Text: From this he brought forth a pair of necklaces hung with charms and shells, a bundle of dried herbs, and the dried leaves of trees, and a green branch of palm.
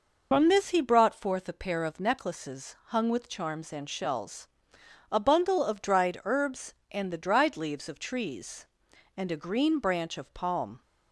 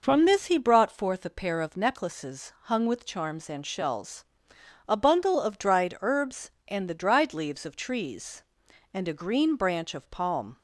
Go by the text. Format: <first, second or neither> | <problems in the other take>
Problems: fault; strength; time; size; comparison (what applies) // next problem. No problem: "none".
second | loses the start of "From"; at 0.3 s; 50 ms